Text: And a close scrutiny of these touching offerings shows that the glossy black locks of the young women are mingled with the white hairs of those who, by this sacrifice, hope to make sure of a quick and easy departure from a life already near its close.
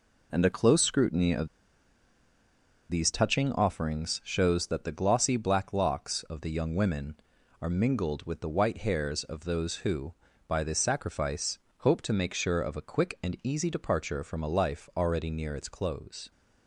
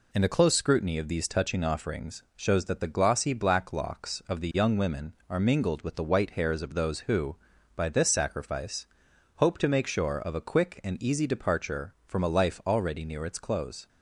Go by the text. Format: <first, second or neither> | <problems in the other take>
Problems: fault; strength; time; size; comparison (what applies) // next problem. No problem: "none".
second | pauses between "of" and "these"; strong; at 1.4 s; 1.4 s long